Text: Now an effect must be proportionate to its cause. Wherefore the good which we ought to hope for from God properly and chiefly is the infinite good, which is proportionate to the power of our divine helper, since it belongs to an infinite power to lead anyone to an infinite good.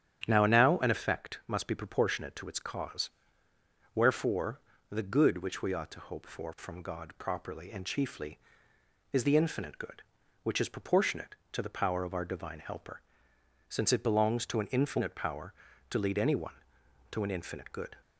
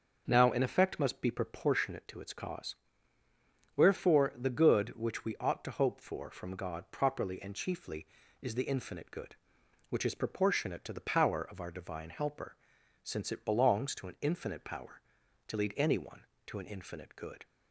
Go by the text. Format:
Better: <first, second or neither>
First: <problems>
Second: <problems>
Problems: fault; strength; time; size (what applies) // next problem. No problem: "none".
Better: second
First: starts louder than the rest; strong; until 1.2 s; 9.5 dB // says "Now" twice; at 0.4 s // pauses between "Wherefore" and "the"; slight; at 4.6 s; 0.28 s long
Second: starts louder than the rest; until 1.2 s; 6.5 dB